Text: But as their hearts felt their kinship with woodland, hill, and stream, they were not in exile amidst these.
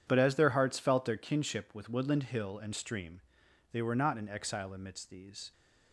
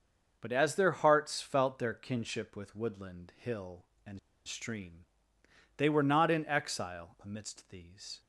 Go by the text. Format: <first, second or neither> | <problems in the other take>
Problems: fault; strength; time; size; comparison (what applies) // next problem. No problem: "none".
first | starts louder than the rest; until 1.4 s; 6.5 dB // pauses between "and" and "stream"; slight; at 4.1 s; 0.28 s long